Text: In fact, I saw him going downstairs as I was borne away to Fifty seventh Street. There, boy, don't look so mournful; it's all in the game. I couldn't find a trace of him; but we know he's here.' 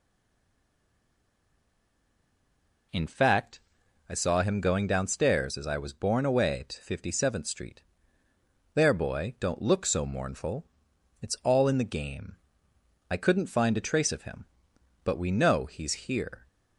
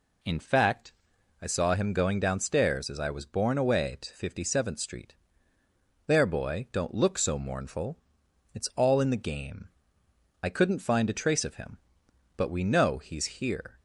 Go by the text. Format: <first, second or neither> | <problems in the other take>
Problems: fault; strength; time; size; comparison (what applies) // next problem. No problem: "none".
second | stays silent before the first word; strong; until 2.9 s; 2.9 s long